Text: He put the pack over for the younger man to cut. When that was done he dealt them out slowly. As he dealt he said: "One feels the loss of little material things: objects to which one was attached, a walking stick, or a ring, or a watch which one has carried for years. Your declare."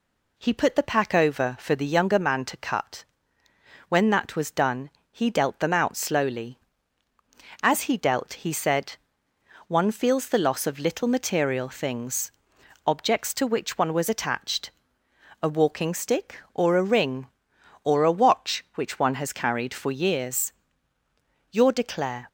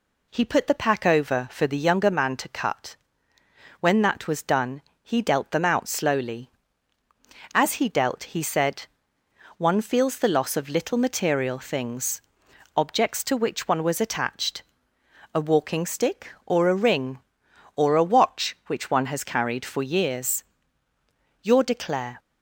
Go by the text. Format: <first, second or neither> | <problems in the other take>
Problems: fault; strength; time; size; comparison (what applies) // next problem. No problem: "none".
neither | pauses between "done" and "he"; slight; the same in both